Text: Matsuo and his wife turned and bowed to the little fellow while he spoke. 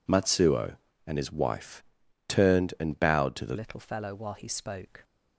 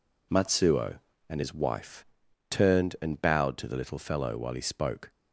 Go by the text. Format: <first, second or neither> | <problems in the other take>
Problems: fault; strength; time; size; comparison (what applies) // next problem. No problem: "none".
second | pauses between "wife" and "turned"; noticeable; at 1.8 s; 0.46 s long; noticeable in the second // changes voice at "little"; from 3.5 s on; 1.5 s long